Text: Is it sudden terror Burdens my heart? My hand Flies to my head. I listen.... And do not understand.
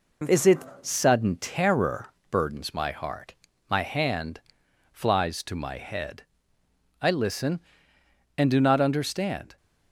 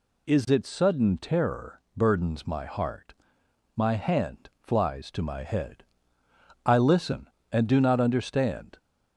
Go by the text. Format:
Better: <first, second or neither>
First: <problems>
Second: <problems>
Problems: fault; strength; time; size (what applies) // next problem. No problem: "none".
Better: second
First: gets quieter; slight; throughout; 2 dB // pauses between "it" and "sudden"; slight; at 0.6 s; 0.22 s long // pauses between "terror" and "Burdens"; slight; at 2.0 s; 0.22 s long // pauses between "hand" and "Flies"; noticeable; at 4.4 s; 0.52 s long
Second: pauses between "terror" and "Burdens"; slight; at 1.8 s; 0.16 s long